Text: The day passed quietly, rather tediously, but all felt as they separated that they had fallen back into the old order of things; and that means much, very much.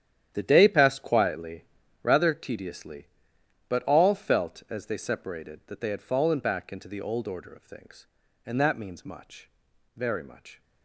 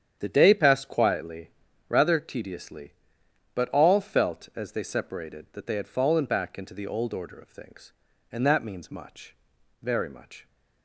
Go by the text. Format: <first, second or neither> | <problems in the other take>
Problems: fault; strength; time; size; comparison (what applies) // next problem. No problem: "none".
second | gets quieter; strong; throughout; 13 dB // starts louder than the rest; strong; until 1.3 s; 10.5 dB; strong in the second